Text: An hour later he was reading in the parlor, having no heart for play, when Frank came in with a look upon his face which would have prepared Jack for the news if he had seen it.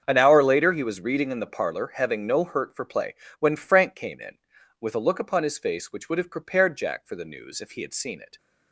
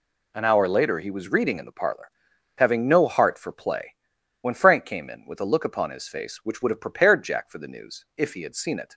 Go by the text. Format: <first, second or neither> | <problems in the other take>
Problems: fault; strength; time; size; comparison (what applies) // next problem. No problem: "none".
second | starts louder than the rest; strong; until 1.0 s; 7.5 dB // says "hurt" for "heart"; at 2.4 s